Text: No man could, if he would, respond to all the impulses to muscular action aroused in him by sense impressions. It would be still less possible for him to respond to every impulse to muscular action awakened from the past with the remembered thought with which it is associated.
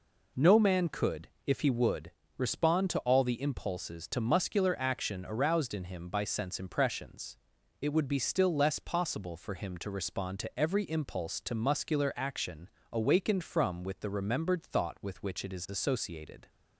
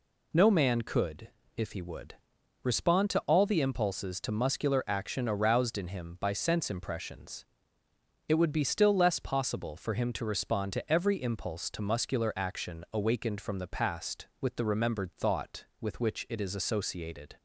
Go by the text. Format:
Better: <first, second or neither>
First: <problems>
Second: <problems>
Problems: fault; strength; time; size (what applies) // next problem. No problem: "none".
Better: second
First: pauses between "action" and "awakened"; slight; at 12.6 s; 0.24 s long // skips "the past"; at 13.8 s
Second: none